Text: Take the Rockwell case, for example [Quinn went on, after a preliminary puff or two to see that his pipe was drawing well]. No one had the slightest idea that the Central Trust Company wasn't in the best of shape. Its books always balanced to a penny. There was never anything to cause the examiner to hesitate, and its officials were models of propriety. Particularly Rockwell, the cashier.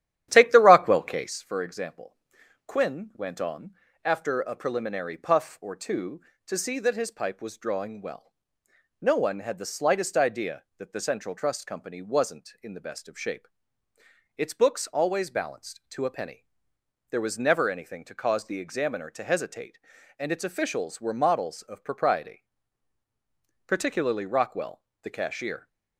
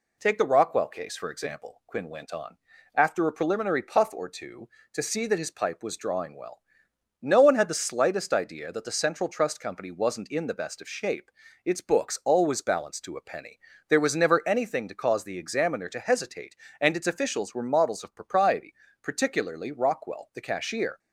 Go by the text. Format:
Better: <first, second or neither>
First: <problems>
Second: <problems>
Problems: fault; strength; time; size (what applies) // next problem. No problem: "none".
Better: second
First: starts louder than the rest; strong; until 1.5 s; 11.5 dB // pauses between "example" and "Quinn"; noticeable; at 2.1 s; 0.52 s long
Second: none